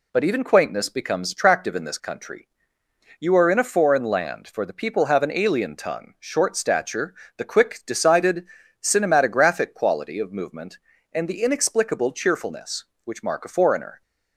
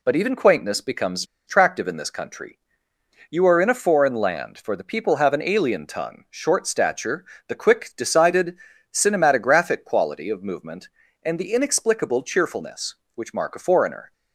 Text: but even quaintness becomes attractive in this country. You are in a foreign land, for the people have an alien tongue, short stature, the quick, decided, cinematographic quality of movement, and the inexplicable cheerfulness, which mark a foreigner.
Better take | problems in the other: first | pauses between "becomes" and "attractive"; slight; at 1.2 s; 0.23 s long

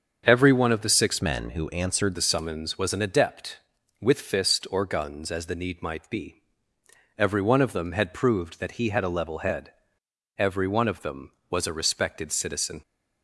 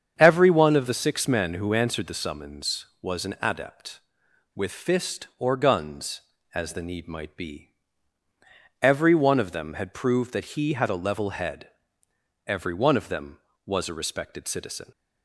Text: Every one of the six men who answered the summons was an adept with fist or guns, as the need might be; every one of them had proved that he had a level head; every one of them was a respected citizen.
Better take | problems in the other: second | starts louder than the rest; until 1.2 s; 7 dB; strong in the second // changes voice from "men" to "answered"; from 1.2 to 2.1 s; 0.9 s long

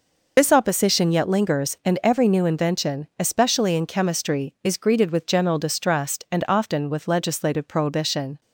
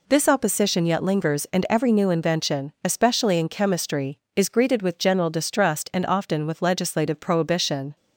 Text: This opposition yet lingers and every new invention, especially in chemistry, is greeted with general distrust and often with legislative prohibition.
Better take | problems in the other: second | loses the start of "This"; at 0.3 s; 50 ms

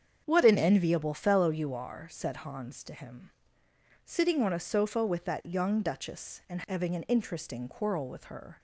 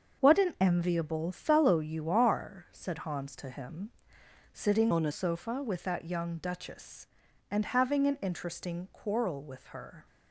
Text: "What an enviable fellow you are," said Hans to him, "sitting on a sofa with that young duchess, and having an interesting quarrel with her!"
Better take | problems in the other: first | starts louder than the rest; until 1.2 s; 6.5 dB; strong in the first // changes voice from "on" to "a"; from 4.9 to 5.1 s; 0.2 s long

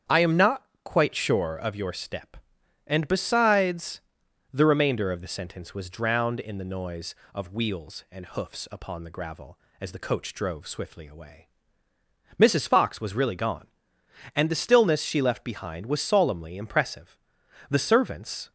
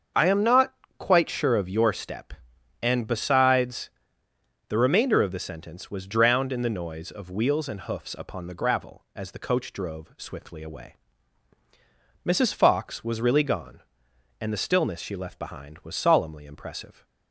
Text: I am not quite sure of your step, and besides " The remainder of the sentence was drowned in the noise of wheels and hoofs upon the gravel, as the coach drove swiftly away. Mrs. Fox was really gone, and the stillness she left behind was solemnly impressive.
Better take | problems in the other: second | starts louder than the rest; strong; until 1.3 s; 8.5 dB; also in the second // pauses between "not" and "quite"; slight; at 0.6 s; 0.22 s long; slight in the second // goes on to say "The servants"; noticeable; from 17.6 s on; 0.82 s long

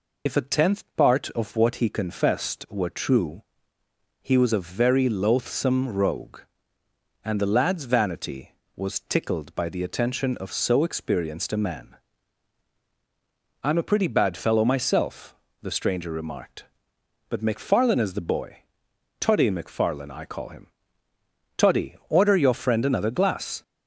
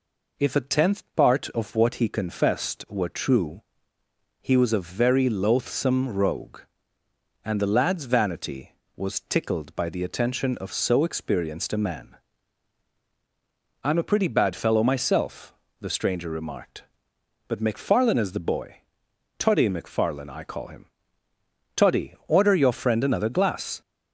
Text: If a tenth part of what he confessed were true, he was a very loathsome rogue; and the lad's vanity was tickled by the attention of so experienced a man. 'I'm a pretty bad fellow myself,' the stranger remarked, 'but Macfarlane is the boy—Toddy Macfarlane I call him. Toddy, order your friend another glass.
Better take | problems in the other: second | loses the start of "If"; at 0.2 s; 65 ms

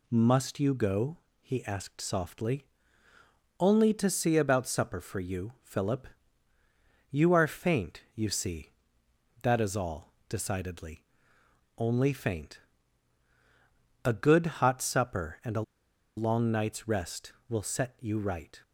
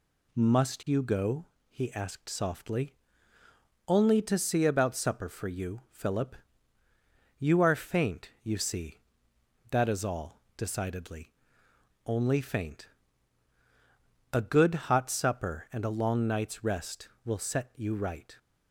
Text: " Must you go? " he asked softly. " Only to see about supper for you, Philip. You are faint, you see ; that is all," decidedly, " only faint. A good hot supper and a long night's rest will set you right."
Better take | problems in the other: second | pauses between "a" and "long"; noticeable; at 15.6 s; 0.55 s long

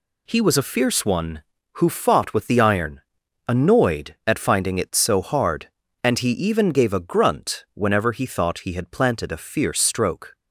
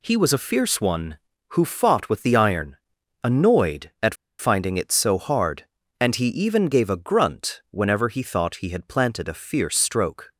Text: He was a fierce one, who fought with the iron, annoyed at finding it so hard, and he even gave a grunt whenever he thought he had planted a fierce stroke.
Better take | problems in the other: first | pauses between "at" and "finding"; slight; at 4.1 s; 0.23 s long

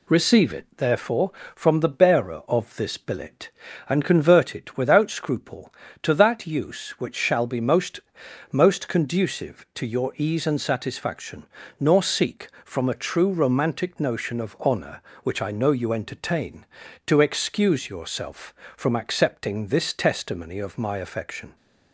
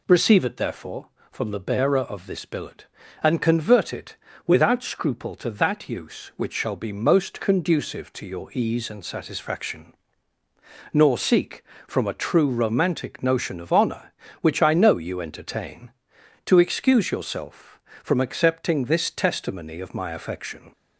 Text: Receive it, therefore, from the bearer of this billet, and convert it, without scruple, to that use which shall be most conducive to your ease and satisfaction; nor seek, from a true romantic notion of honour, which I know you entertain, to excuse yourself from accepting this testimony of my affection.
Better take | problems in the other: second | says "most" twice; at 8.5 s

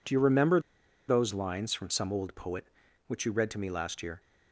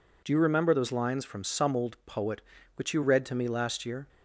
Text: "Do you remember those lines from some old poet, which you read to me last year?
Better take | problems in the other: second | pauses between "remember" and "those"; noticeable; at 0.5 s; 0.48 s long

